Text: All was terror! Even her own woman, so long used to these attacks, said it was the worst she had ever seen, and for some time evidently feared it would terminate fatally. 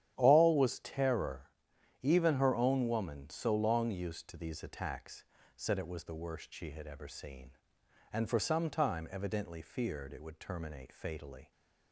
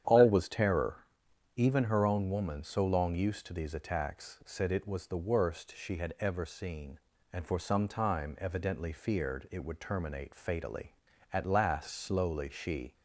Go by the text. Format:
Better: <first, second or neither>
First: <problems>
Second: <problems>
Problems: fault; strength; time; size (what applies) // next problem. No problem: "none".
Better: first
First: starts louder than the rest; strong; until 1.1 s; 10.5 dB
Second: starts louder than the rest; strong; until 1.6 s; 9.5 dB // goes on to say "At last slowly she"; from 11.3 s on; 1.6 s long